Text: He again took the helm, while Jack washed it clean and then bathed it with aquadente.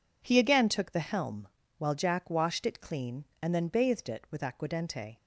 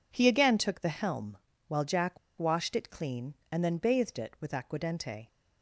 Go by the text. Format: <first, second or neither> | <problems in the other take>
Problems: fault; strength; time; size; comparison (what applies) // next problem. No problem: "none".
first | pauses between "Jack" and "washed"; slight; at 2.1 s; 0.20 s long